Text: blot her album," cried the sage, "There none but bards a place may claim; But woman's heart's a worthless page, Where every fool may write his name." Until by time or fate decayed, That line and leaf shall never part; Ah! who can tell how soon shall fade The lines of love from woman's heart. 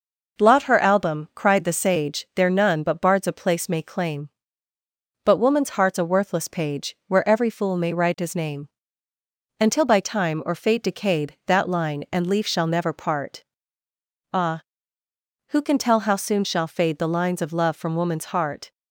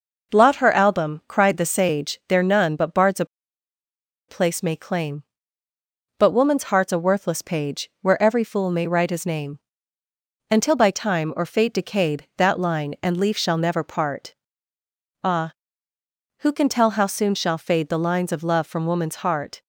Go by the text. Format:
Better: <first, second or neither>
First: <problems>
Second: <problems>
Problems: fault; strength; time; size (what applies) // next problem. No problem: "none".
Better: first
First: none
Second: pauses between "a" and "place"; at 3.2 s; 1.0 s long